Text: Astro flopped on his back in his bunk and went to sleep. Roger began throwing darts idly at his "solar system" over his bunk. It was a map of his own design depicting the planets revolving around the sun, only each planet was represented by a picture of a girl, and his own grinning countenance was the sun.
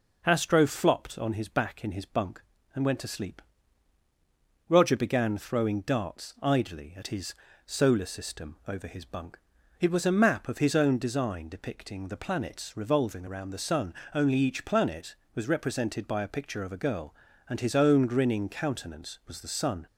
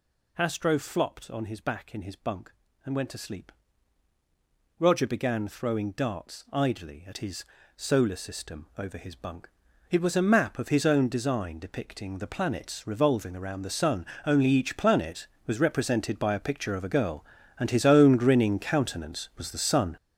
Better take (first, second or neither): first